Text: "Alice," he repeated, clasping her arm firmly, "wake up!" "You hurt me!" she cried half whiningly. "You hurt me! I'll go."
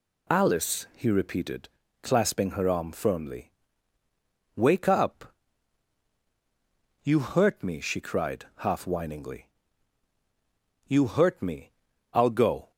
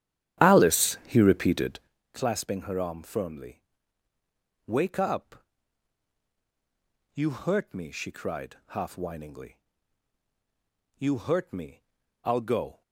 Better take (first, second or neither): first